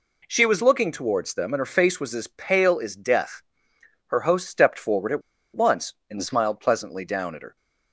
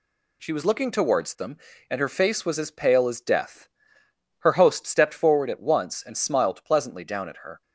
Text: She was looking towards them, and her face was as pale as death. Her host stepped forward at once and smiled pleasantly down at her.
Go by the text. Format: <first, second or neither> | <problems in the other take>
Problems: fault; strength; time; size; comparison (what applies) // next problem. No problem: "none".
second | pauses between "at" and "once"; slight; at 5.2 s; 0.34 s long